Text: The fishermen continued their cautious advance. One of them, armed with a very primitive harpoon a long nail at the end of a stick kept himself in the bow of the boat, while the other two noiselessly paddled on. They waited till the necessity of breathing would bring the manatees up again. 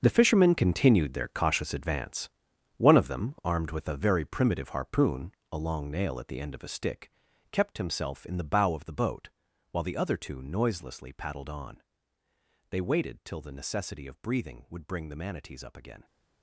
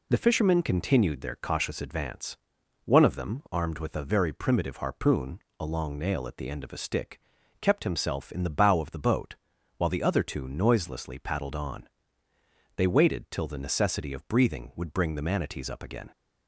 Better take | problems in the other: second | gets quieter; strong; throughout; 13.5 dB // pauses between "harpoon" and "a"; slight; at 5.3 s; 0.20 s long; slight in the second // pauses between "stick" and "kept"; at 7.1 s; 0.40 s long; also in the second

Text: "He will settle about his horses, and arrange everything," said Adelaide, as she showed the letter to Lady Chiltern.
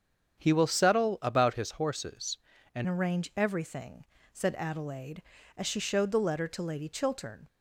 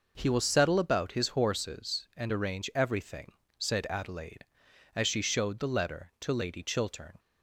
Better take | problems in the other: second | starts louder than the rest; strong; until 1.4 s; 8 dB // changes voice at "arrange"; from 2.8 s on; 4.6 s long

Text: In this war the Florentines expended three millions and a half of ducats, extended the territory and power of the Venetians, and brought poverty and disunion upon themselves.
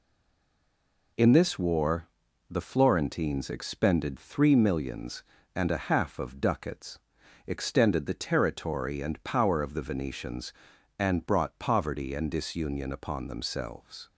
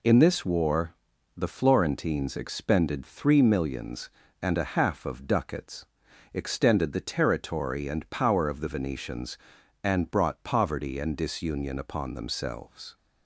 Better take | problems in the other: second | stays silent before the first word; until 1.1 s; 1.1 s long // pauses between "war" and "the"; at 2.0 s; 0.42 s long; also in the second

